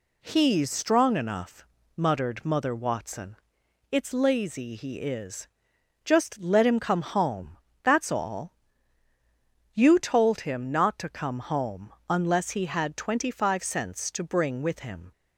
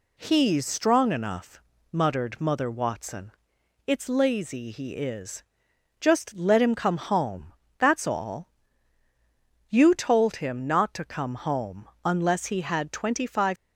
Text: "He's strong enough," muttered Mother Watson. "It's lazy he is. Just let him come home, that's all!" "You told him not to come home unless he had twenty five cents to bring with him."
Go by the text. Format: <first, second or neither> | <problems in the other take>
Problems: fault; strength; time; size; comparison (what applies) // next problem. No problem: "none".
first | pauses between "home" and "unless"; slight; at 11.8 s; 0.16 s long; slight in the first // stops before "cents to bring with him"; at 13.5 s